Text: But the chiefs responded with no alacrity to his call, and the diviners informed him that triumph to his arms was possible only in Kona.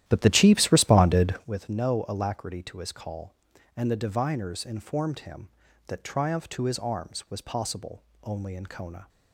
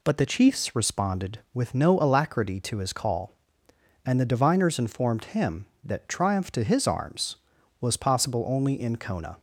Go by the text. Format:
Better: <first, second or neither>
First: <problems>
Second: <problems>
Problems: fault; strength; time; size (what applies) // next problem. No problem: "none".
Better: second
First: starts louder than the rest; strong; until 1.6 s; 12.5 dB // pauses between "possible" and "only"; slight; at 8.0 s; 0.20 s long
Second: none